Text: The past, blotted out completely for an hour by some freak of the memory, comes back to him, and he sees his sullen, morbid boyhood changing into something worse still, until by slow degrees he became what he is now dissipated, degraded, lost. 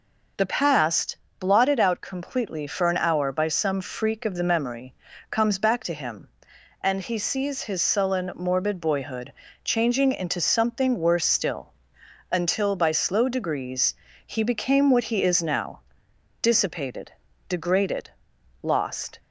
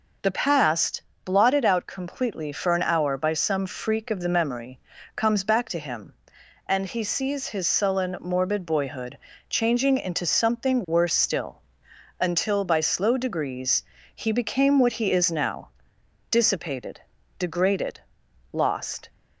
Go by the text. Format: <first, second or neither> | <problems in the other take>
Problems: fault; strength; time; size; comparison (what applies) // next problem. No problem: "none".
neither | pauses between "boyhood" and "changing"; slight; the same in both // pauses between "degrees" and "he"; slight; the same in both // pauses between "now" and "dissipated"; noticeable; the same in both